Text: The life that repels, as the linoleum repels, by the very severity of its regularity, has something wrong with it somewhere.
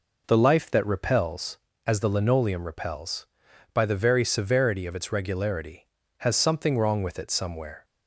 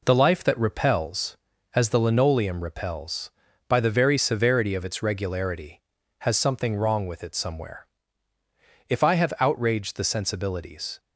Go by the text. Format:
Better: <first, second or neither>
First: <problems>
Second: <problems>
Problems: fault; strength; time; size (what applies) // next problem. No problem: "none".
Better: first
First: none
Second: goes on to say "If I have outraged the sensibilities"; strong; from 8.8 s on; 2.1 s long